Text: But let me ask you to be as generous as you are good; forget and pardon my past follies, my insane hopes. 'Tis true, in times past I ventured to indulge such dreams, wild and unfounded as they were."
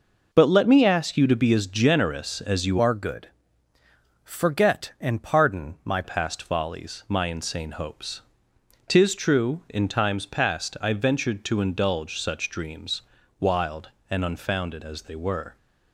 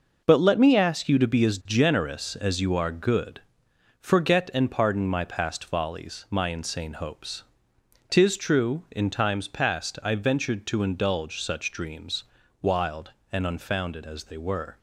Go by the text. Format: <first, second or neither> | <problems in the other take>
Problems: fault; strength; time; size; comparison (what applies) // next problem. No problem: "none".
second | changes voice from "are" to "my"; from 2.7 to 6.0 s; 3.3 s long